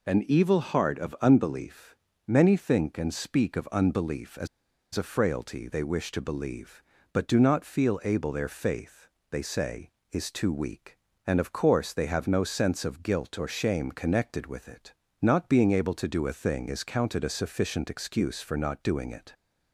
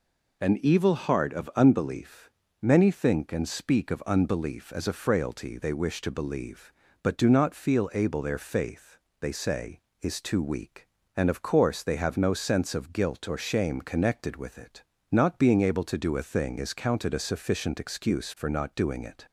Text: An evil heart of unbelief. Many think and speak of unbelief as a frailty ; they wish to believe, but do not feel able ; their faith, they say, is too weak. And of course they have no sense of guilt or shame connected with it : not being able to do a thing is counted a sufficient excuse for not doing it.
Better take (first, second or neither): second